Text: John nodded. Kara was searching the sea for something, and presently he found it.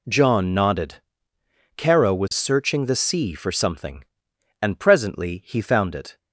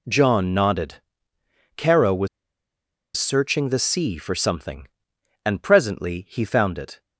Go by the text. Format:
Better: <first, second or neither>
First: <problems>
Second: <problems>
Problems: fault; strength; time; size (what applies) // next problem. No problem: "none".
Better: first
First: none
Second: pauses between "was" and "searching"; noticeable; at 2.2 s; 0.88 s long